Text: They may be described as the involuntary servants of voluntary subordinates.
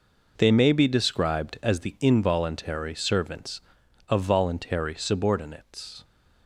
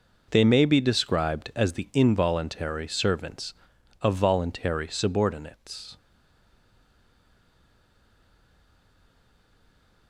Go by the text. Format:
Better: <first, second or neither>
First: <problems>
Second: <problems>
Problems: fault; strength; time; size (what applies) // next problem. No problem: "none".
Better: first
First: none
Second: stays silent after the last word; strong; from 5.9 s on; 4.1 s long